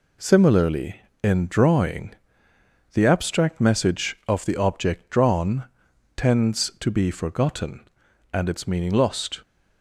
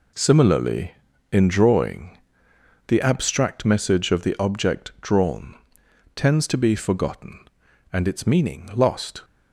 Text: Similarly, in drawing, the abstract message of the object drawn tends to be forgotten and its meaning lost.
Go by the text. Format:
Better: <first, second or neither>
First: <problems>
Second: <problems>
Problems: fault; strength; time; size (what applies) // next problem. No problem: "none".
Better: first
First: pauses between "drawn" and "tends"; noticeable; at 5.6 s; 0.54 s long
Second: gets quieter; strong; throughout; 8.5 dB // pauses between "drawn" and "tends"; noticeable; at 5.5 s; 0.58 s long